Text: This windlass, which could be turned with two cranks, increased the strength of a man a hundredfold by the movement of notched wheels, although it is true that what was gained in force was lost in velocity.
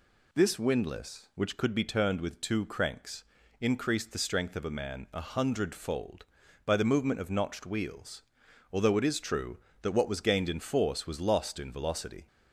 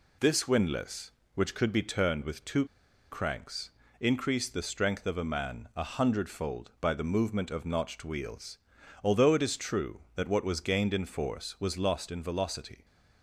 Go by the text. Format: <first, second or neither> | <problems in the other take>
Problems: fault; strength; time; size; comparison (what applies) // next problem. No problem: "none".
first | pauses between "two" and "cranks"; noticeable; at 2.6 s; 0.47 s long